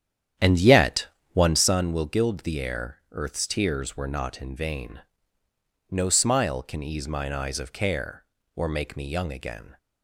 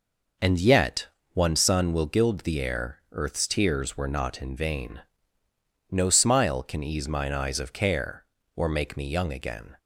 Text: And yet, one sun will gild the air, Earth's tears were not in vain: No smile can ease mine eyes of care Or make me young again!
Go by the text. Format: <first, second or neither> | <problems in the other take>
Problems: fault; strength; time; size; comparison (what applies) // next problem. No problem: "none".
second | starts louder than the rest; strong; until 1.8 s; 10 dB